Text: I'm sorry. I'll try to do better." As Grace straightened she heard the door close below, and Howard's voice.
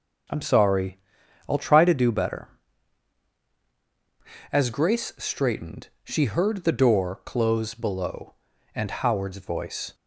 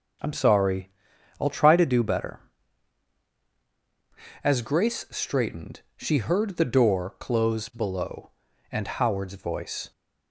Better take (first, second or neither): neither